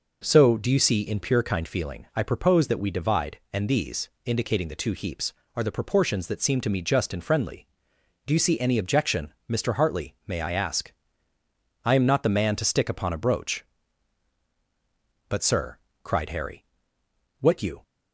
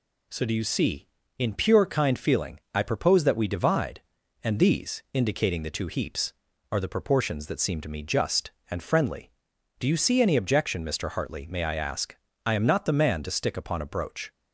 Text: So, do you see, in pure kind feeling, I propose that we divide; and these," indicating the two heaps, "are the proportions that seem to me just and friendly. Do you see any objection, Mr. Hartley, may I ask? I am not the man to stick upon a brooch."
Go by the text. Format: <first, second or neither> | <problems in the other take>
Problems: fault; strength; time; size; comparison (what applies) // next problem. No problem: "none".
second | goes on to say "But sir cried Harry what you"; strong; from 15.2 s on; 2.5 s long